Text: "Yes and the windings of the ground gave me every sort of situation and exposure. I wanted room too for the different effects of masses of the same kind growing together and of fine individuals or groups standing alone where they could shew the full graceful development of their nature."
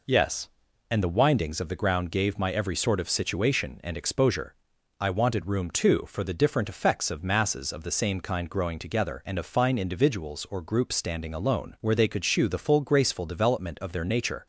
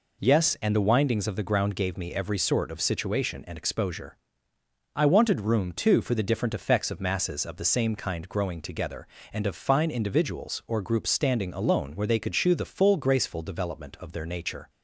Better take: second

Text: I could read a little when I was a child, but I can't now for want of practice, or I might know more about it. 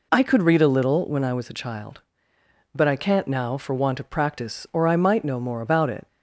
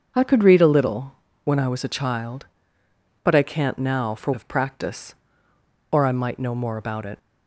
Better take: first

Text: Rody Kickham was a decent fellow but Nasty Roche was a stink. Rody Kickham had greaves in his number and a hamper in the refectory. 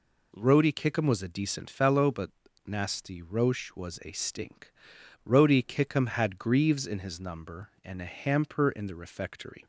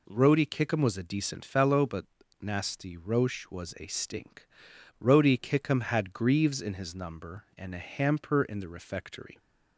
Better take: neither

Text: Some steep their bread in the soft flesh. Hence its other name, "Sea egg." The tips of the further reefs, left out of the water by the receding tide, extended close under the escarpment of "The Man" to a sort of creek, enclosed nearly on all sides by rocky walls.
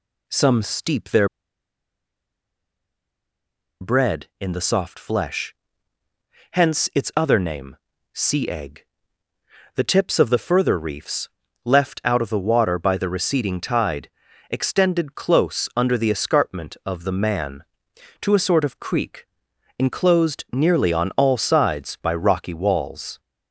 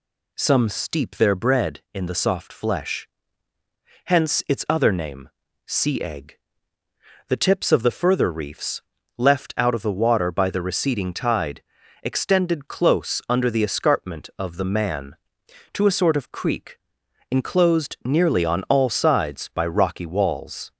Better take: second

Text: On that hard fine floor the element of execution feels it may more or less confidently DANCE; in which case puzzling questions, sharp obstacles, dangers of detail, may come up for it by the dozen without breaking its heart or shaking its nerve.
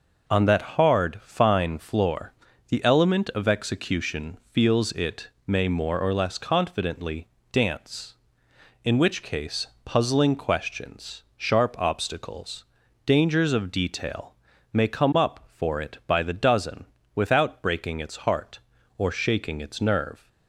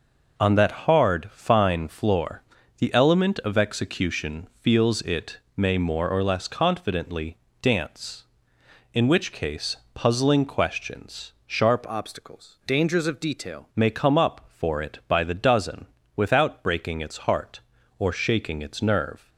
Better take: first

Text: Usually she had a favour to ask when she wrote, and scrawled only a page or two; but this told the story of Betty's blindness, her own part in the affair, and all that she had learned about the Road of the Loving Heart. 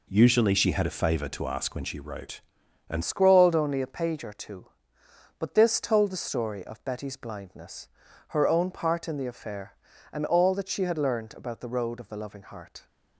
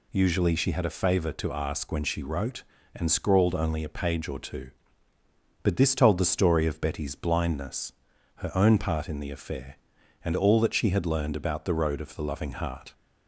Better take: second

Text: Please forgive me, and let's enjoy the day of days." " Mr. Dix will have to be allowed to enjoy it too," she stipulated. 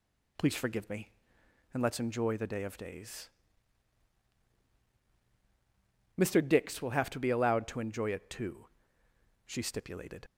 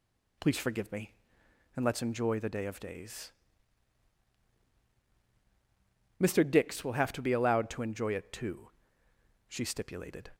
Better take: second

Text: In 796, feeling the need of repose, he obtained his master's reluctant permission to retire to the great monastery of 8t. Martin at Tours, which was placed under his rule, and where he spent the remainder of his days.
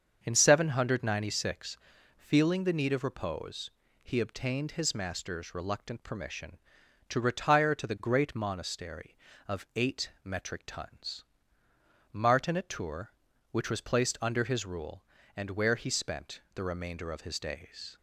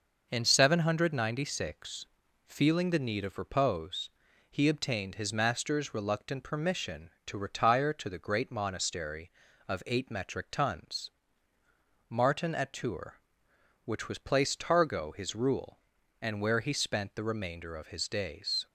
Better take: first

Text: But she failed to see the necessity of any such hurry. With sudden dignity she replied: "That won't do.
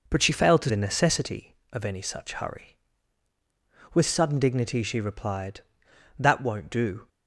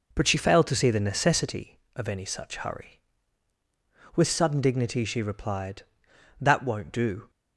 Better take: second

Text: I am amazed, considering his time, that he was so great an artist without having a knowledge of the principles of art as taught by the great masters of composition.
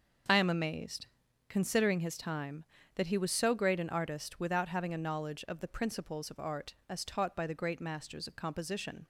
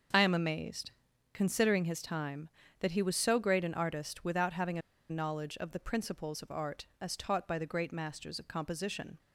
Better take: first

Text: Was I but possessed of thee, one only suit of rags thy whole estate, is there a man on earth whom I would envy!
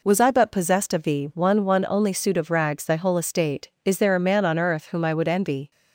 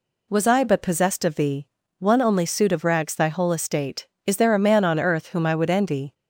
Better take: second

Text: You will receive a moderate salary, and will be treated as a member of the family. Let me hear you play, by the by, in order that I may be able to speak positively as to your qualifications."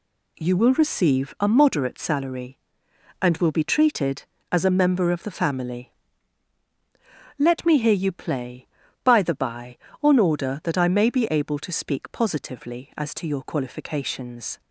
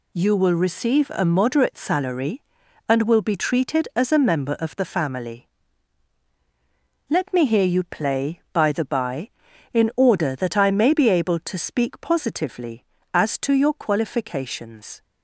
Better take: second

